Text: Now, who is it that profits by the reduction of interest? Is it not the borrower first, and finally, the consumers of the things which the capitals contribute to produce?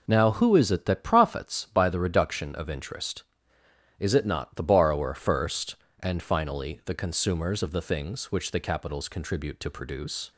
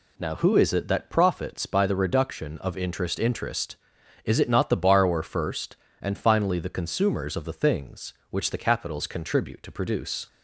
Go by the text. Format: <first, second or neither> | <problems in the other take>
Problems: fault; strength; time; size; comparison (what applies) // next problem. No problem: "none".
first | says "interest" twice; at 3.1 s